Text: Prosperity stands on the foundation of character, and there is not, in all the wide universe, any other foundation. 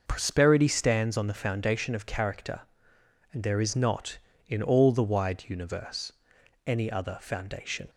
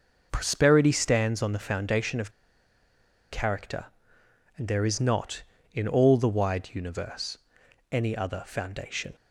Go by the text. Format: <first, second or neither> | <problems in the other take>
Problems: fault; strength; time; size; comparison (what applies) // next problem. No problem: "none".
first | pauses between "of" and "character"; at 2.3 s; 1.0 s long